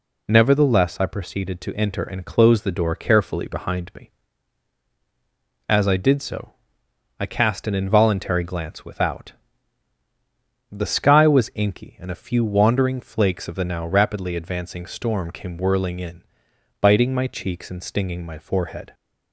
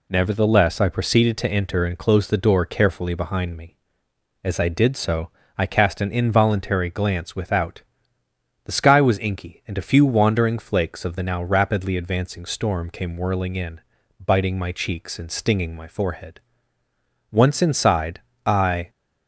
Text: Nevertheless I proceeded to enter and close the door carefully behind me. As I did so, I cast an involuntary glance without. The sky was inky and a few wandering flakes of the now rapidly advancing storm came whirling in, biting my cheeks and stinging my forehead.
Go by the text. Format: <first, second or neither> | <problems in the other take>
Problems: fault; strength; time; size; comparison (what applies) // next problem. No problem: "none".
first | goes on to say "Once inside I"; from 17.2 s on; 1.6 s long